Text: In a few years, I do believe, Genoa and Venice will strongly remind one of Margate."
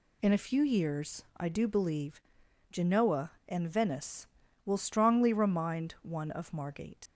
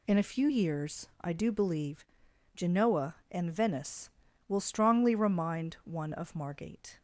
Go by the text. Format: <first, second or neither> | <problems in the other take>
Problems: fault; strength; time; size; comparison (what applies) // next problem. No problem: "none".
second | leaves "Margate" unfinished; at 7.0 s; 115 ms